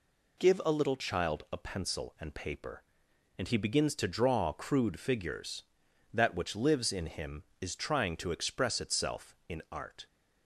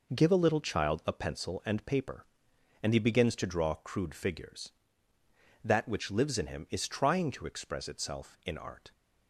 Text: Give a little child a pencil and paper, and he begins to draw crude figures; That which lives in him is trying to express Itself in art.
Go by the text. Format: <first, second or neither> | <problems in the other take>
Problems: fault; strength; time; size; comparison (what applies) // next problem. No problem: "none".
neither | none